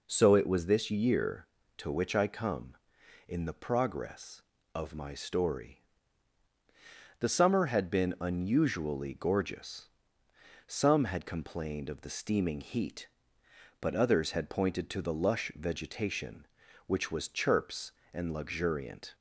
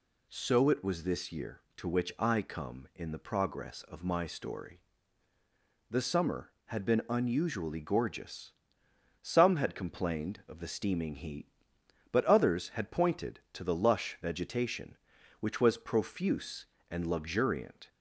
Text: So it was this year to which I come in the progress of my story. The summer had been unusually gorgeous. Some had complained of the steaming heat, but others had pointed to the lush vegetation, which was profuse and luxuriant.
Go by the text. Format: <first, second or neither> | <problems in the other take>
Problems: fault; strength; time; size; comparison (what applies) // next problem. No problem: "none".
second | says "chirps" for "profuse"; at 17.2 s